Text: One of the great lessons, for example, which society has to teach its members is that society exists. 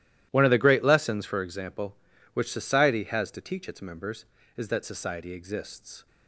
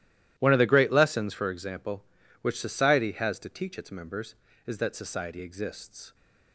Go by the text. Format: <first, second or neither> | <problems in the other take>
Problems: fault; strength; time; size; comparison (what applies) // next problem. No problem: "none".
neither | starts louder than the rest; strong; the same in both